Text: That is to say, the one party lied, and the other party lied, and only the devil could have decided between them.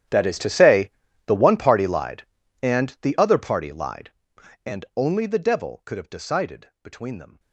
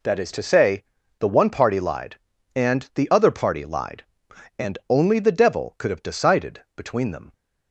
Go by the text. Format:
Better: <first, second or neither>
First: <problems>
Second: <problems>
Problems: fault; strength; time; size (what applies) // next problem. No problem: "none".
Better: second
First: gets quieter; strong; throughout; 21 dB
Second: none